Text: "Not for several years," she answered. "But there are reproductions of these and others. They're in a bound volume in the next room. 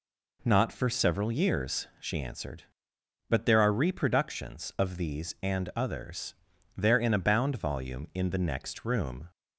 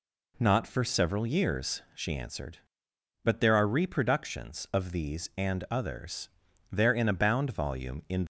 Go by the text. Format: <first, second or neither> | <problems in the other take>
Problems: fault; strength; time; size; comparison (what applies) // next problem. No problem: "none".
first | stops before "the next room"; at 8.2 s